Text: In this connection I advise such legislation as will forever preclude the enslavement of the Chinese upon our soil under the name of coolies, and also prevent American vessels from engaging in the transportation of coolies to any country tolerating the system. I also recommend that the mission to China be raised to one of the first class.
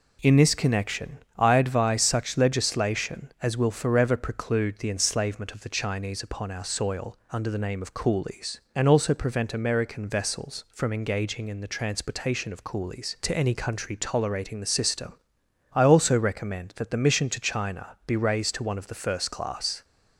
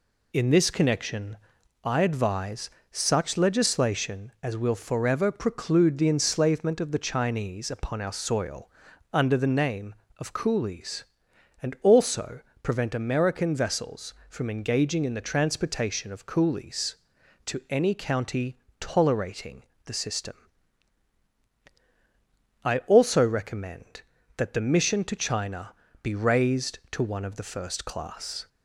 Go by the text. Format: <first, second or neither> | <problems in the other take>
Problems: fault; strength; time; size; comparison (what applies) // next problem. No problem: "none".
first | pauses between "connection" and "I"; noticeable; at 1.3 s; 0.46 s long; slight in the first // pauses between "advise" and "such"; slight; at 2.6 s; 0.22 s long // pauses between "soil" and "under"; at 8.6 s; 0.42 s long // pauses between "also" and "prevent"; slight; at 12.4 s; 0.20 s long // says "county" for "country"; at 17.9 s // pauses between "tolerating" and "the"; slight; at 19.6 s; 0.24 s long // pauses between "China" and "be"; slight; at 25.7 s; 0.30 s long